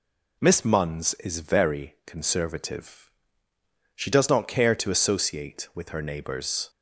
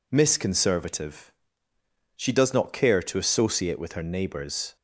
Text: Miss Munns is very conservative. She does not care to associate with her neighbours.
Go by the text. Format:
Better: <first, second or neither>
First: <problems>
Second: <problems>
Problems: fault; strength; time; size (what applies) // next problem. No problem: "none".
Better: first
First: none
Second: skips "Munns is very"; at 0.3 s